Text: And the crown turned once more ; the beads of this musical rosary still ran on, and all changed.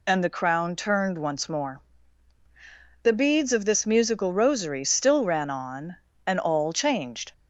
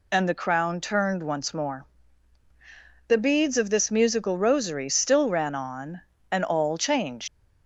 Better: first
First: none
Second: leaves "changed" unfinished; at 7.2 s; 95 ms

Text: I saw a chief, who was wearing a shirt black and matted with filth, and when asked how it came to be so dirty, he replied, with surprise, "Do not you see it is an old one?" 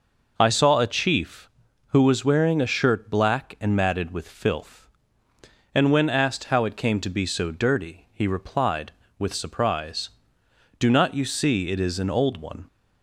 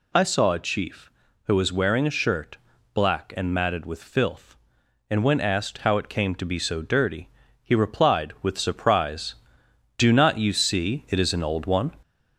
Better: first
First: none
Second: gets louder; slight; throughout; 2.5 dB // pauses between "shirt" and "black"; slight; at 2.5 s; 0.36 s long

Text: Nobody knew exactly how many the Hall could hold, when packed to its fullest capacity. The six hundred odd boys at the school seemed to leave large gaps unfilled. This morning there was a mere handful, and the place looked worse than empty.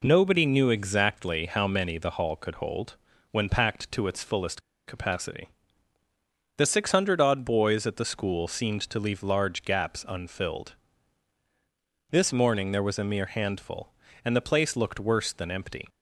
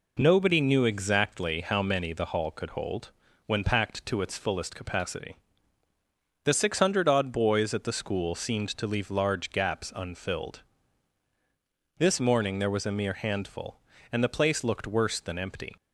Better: second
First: pauses between "fullest" and "capacity"; slight; at 4.6 s; 0.26 s long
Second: none

